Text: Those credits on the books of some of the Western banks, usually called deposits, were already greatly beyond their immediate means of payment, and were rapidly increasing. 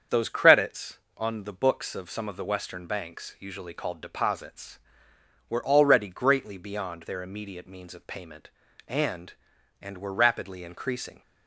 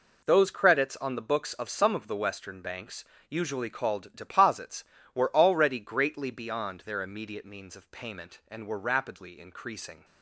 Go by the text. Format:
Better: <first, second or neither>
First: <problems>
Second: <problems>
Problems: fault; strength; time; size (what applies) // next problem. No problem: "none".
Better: second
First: starts louder than the rest; strong; until 1.2 s; 7.5 dB // says "and" twice; at 9.8 s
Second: none